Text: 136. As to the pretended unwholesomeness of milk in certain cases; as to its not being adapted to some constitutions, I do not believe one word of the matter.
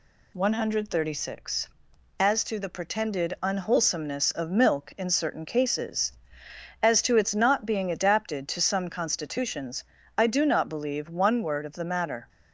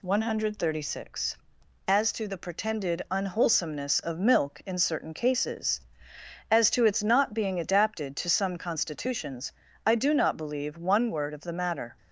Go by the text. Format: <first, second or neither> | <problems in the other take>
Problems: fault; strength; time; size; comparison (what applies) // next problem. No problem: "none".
neither | none